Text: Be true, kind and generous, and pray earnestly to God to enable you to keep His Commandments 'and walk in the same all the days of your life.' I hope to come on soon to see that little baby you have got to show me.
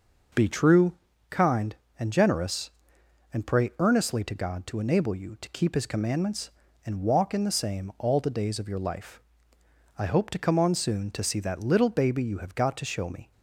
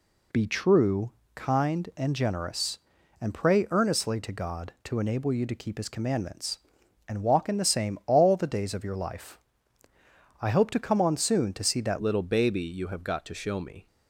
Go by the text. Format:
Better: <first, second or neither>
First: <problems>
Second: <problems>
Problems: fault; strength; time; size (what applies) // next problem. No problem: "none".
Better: first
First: none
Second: changes voice at "little"; from 12.0 s on; 1.8 s long